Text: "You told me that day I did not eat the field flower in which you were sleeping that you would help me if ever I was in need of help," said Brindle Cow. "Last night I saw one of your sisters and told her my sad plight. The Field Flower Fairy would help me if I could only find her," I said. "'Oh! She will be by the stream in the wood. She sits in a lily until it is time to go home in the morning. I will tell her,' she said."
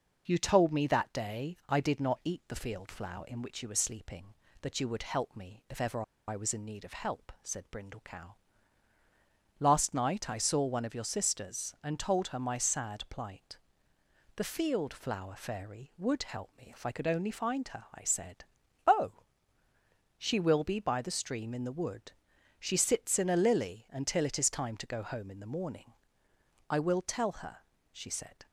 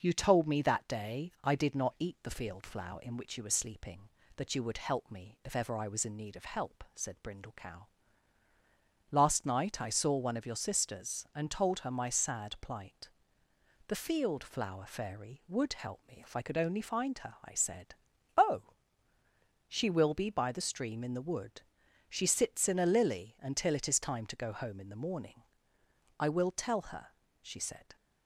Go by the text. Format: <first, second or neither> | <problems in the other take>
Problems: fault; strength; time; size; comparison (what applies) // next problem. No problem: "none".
second | pauses between "ever" and "I"; slight; at 6.0 s; 0.25 s long